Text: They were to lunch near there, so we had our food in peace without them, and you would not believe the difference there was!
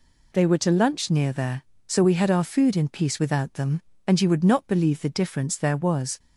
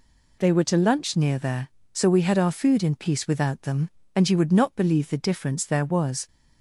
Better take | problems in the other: neither | none

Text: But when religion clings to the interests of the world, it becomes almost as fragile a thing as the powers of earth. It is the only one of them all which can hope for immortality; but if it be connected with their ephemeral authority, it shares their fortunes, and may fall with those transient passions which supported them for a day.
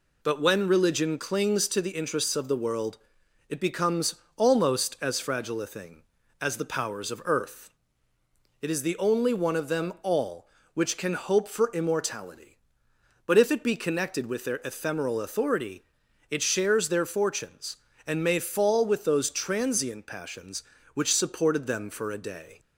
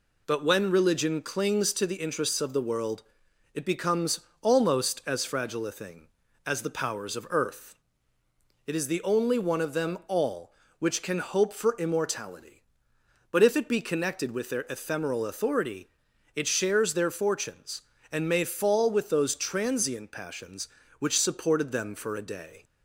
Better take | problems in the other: neither | pauses between "becomes" and "almost"; slight; the same in both

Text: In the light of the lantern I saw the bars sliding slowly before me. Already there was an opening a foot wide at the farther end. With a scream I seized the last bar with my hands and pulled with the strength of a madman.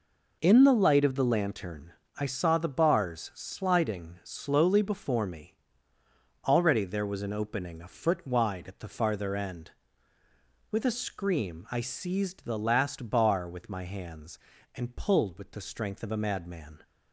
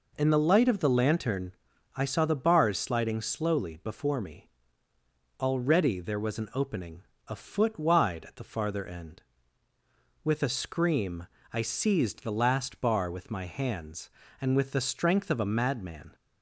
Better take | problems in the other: first | pauses between "lantern" and "I"; at 1.5 s; 0.44 s long; slight in the first // pauses between "opening" and "a"; slight; at 7.0 s; 0.26 s long // pauses between "scream" and "I"; slight; at 11.2 s; 0.24 s long // skips "pulled"; at 14.5 s

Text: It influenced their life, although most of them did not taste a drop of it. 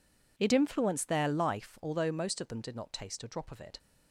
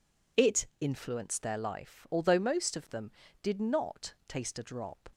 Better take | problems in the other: first | stops before "of it"; at 5.1 s

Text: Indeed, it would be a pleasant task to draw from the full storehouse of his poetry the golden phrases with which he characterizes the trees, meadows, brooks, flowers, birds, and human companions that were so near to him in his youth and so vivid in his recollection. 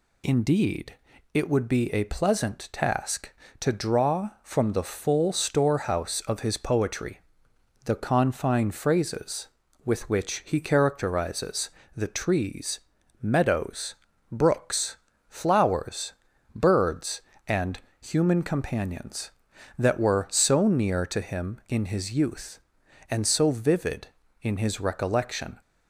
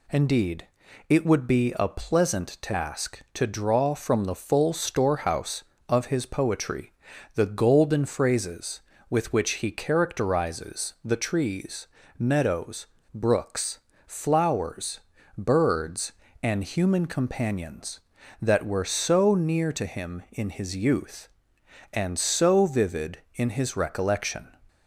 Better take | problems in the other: second | pauses between "poetry" and "the"; noticeable; at 7.1 s; 0.66 s long; also in the second // says "confine" for "golden"; at 7.9 s // pauses between "characterizes" and "the"; slight; at 11.6 s; 0.24 s long // pauses between "and" and "human"; slight; at 17.7 s; 0.20 s long

